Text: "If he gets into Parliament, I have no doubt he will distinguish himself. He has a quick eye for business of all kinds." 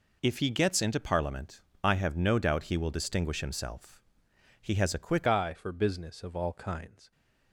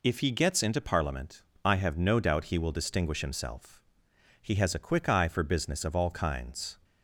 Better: second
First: changes voice at "eye"; from 5.2 s on; 1.9 s long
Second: none

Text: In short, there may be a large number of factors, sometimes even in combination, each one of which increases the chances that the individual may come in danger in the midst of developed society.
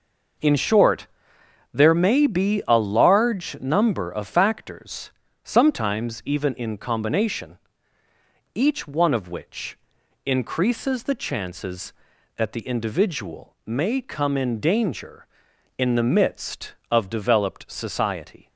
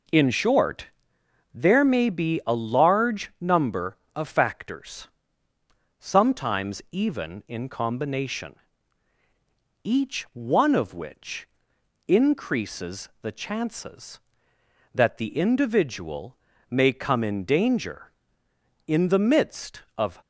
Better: first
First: pauses between "which" and "increases"; noticeable; at 9.7 s; 0.48 s long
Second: pauses between "which" and "increases"; noticeable; at 11.4 s; 0.60 s long // pauses between "individual" and "may"; slight; at 16.3 s; 0.34 s long // stops before "developed society"; at 20.2 s

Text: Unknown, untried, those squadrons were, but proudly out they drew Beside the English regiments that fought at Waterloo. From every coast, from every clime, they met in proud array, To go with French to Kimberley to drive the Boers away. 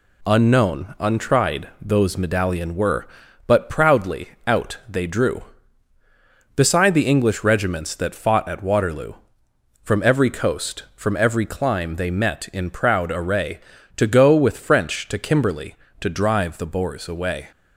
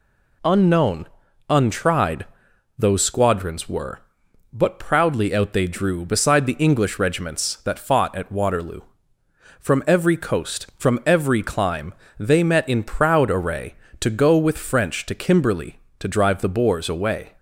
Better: second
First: says "medallion" for "squadrons"; at 2.1 s // pauses between "proudly" and "out"; slight; at 4.2 s; 0.16 s long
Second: none

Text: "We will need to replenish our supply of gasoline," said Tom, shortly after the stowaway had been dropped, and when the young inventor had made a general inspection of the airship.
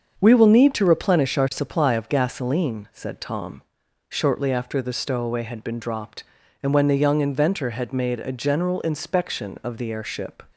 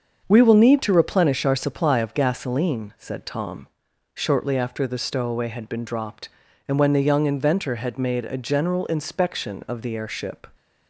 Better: neither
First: starts louder than the rest; until 1.2 s; 7 dB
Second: starts louder than the rest; until 1.2 s; 7 dB

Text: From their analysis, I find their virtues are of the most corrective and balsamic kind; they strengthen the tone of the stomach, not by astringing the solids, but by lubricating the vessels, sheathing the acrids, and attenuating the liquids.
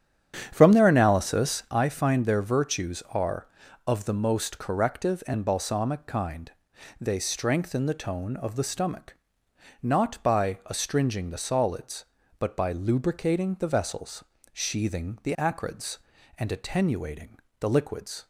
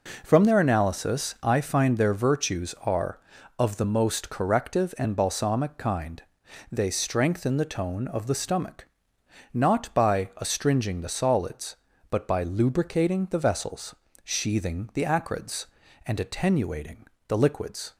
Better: second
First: starts louder than the rest; strong; until 1.8 s; 9 dB // pauses between "attenuating" and "the"; slight; at 17.3 s; 0.20 s long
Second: pauses between "attenuating" and "the"; slight; at 17.0 s; 0.20 s long

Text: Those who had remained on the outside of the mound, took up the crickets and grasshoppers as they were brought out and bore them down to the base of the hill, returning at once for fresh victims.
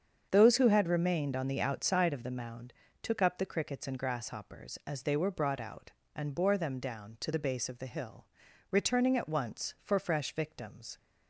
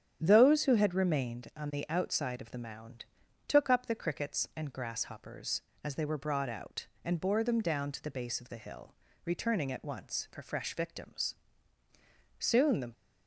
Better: first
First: starts louder than the rest; strong; until 1.3 s; 7 dB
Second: starts louder than the rest; strong; until 1.2 s; 9.5 dB // goes on to say "Soon the"; from 12.3 s on; 0.54 s long

